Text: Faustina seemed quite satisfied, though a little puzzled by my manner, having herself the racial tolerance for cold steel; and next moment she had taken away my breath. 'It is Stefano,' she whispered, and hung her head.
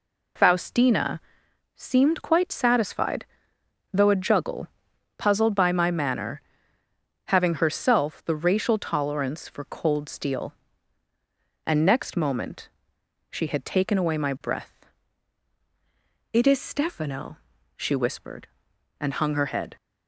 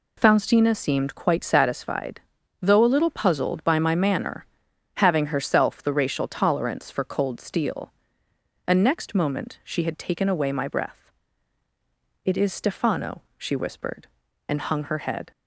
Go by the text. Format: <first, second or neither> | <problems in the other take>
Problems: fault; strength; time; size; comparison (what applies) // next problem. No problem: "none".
second | pauses between "Faustina" and "seemed"; noticeable; at 1.1 s; 0.56 s long // says "juggle" for "little"; at 4.1 s // pauses between "moment" and "she"; noticeable; at 12.6 s; 0.62 s long